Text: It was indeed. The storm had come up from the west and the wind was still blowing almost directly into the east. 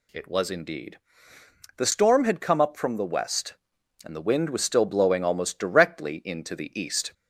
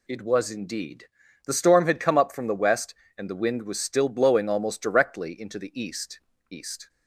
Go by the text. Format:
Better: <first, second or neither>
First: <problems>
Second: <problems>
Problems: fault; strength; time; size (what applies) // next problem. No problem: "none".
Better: first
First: none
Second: says "east" twice; at 6.4 s